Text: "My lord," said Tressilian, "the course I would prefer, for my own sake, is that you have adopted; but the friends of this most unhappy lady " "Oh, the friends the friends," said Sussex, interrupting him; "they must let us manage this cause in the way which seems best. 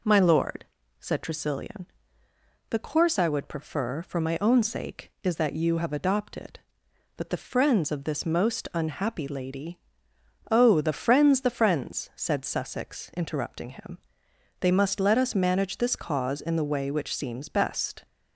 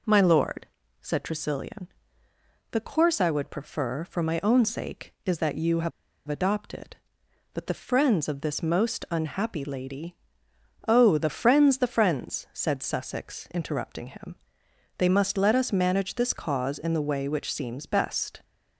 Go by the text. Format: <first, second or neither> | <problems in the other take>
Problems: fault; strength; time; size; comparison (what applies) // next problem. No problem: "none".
first | pauses between "have" and "adopted"; at 5.9 s; 0.37 s long